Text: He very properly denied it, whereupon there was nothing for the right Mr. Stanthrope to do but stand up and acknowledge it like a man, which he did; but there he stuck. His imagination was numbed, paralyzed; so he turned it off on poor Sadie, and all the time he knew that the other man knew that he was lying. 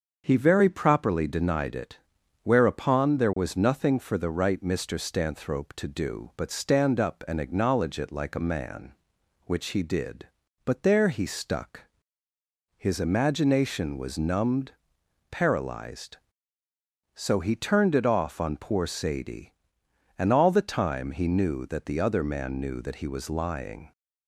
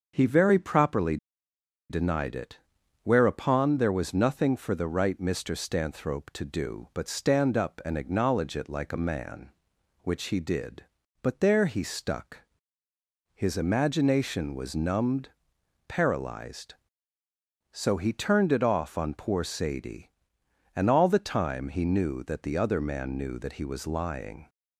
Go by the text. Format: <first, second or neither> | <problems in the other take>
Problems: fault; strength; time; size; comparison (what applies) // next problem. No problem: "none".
first | starts louder than the rest; until 1.1 s; 6.5 dB; also in the first // pauses between "properly" and "denied"; noticeable; at 1.1 s; 0.73 s long